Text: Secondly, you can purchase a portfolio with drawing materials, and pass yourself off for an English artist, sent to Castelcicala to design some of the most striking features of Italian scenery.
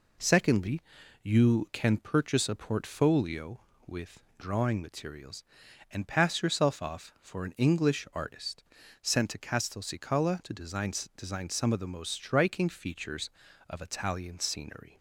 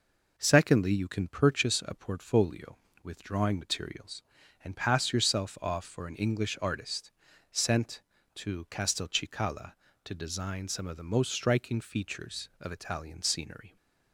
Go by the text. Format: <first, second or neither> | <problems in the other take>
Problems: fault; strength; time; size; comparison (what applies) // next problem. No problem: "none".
second | says "design" twice; at 11.1 s